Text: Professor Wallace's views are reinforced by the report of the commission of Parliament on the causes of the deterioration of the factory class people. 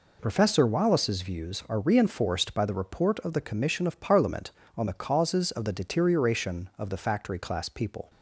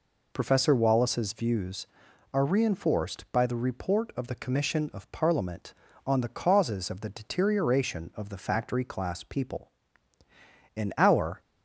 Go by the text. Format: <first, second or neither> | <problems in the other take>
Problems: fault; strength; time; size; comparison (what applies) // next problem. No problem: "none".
first | goes on to say "In our"; noticeable; from 10.7 s on; 0.64 s long